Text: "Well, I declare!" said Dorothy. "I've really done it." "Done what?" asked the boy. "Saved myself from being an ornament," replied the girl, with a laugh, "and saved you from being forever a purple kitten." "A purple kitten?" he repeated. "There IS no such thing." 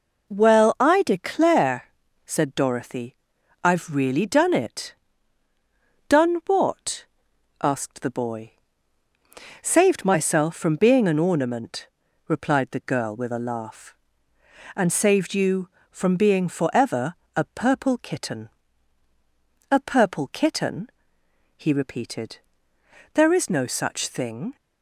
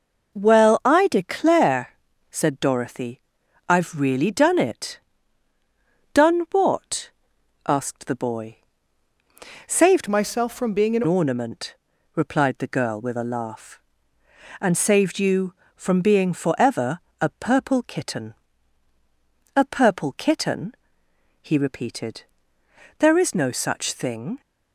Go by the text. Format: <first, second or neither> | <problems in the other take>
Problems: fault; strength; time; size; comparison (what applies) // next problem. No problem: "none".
first | changes voice from "myself" to "an"; from 10.0 to 11.0 s; 1.0 s long // pauses between "forever" and "a"; slight; at 17.0 s; 0.20 s long; slight in the first